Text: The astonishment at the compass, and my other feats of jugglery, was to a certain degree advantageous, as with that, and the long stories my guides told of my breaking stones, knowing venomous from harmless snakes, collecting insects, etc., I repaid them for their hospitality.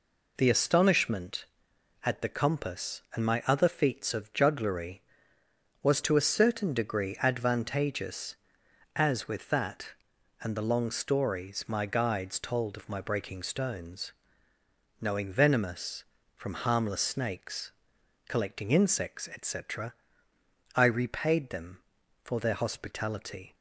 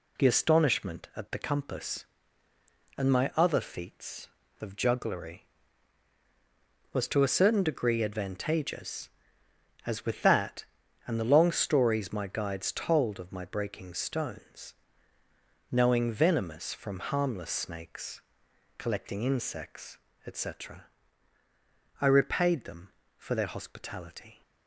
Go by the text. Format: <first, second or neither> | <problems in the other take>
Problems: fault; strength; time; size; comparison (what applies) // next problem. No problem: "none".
neither | none